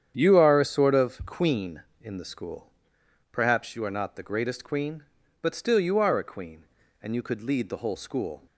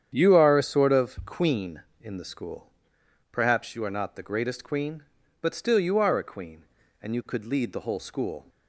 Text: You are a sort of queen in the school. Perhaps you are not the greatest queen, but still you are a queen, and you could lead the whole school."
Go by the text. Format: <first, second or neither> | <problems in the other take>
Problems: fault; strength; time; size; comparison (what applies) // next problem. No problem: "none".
neither | starts louder than the rest; strong; the same in both